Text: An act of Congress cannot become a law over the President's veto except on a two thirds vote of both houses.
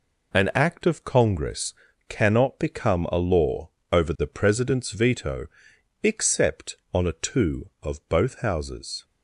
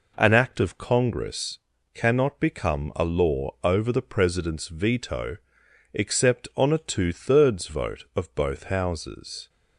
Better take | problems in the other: second | pauses between "Congress" and "cannot"; slight; at 1.7 s; 0.34 s long; also in the second // pauses between "law" and "over"; slight; at 3.6 s; 0.24 s long // pauses between "veto" and "except"; noticeable; at 5.4 s; 0.56 s long; noticeable in the second // skips "thirds vote"; at 7.7 s

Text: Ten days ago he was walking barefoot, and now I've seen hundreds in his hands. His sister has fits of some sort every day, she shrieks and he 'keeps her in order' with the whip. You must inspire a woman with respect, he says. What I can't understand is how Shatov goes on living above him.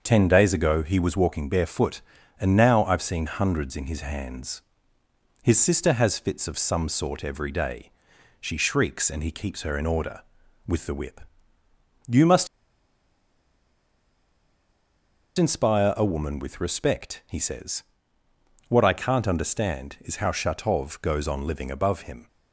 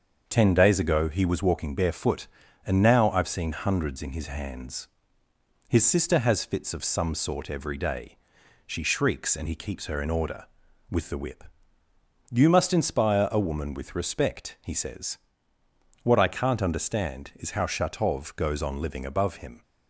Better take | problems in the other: second | starts louder than the rest; until 1.0 s; 6.5 dB; also in the second // pauses between "must" and "inspire"; strong; at 12.4 s; 2.9 s long

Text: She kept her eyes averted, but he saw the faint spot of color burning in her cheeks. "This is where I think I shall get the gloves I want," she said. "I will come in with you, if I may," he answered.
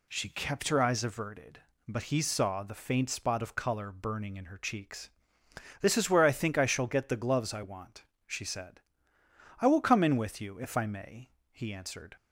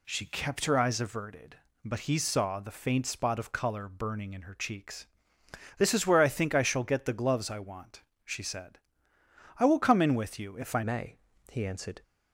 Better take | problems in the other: first | changes voice at "may"; from 10.8 s on; 1.2 s long

